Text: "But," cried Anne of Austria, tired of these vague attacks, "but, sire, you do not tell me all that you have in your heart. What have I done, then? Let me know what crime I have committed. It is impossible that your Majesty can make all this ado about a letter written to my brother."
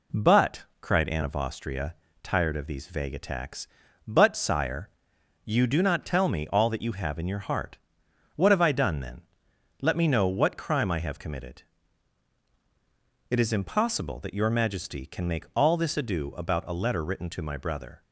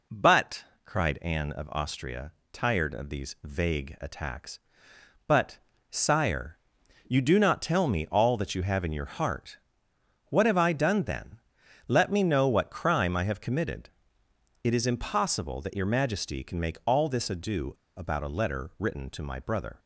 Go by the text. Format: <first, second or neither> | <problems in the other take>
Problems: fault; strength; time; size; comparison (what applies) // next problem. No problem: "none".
first | pauses between "ado" and "about"; slight; at 17.7 s; 0.24 s long